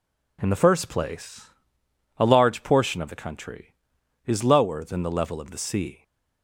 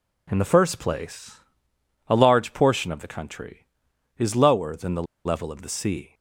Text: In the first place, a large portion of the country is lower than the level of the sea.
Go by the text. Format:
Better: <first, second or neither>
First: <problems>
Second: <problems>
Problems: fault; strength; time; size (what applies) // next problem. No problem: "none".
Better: first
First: none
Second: pauses between "the" and "level"; slight; at 5.0 s; 0.21 s long